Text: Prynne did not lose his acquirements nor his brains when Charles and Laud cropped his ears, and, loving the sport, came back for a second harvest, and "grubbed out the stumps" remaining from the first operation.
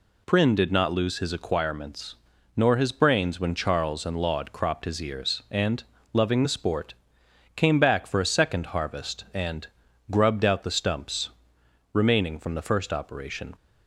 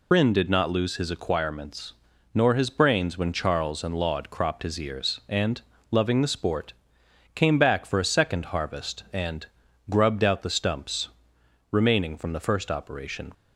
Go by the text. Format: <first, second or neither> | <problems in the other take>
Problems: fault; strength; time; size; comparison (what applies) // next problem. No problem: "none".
first | loses the start of "Prynne"; at 0.1 s; 70 ms // pauses between "acquirements" and "nor"; at 1.9 s; 0.40 s long; also in the first // pauses between "and" and "grubbed"; at 9.4 s; 0.44 s long; also in the first // pauses between "stumps" and "remaining"; noticeable; at 11.0 s; 0.61 s long; noticeable in the first